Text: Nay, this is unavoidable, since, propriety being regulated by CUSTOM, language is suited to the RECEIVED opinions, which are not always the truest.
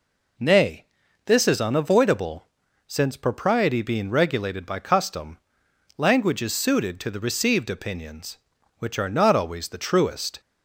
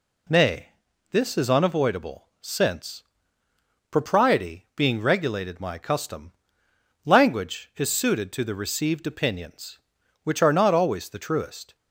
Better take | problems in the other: first | says "my" for "by"; at 5.6 s

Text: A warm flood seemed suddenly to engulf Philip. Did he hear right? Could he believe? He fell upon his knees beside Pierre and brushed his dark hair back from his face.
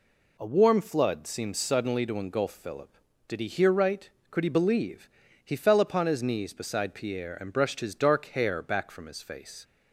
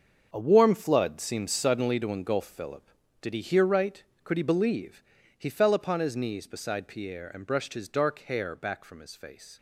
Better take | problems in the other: first | gets quieter; strong; throughout; 11.5 dB

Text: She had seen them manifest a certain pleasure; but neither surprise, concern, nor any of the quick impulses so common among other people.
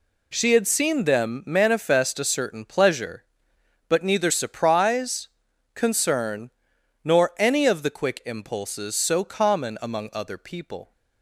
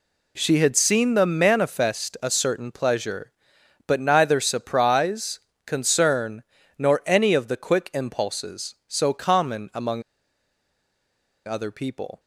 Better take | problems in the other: first | pauses between "among" and "other"; strong; at 10.0 s; 1.4 s long

